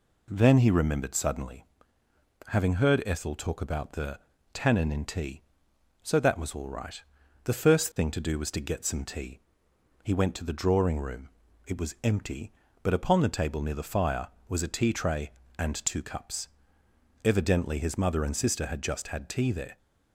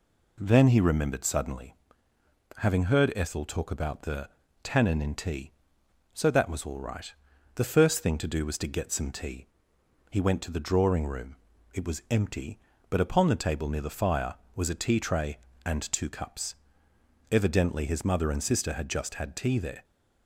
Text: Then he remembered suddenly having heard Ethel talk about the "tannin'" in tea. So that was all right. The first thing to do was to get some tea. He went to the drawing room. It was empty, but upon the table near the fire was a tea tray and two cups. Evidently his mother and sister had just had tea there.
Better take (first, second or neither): neither